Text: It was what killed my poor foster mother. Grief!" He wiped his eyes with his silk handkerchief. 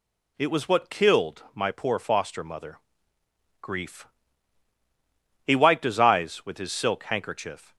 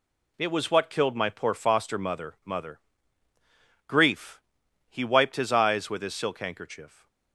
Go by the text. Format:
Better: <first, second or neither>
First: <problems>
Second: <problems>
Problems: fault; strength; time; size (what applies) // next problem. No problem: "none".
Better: first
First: none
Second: says "mother" twice; at 2.4 s